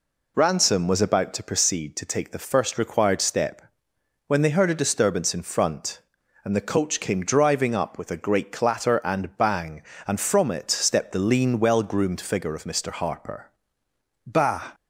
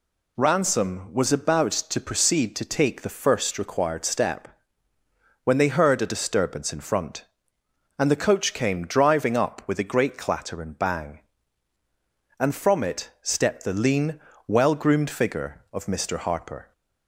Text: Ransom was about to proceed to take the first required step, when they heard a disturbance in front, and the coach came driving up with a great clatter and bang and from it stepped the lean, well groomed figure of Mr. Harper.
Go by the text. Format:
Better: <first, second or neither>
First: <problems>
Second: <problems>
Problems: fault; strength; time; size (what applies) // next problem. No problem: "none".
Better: second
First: goes on to say "Bah"; slight; from 14.2 s on; 0.46 s long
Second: none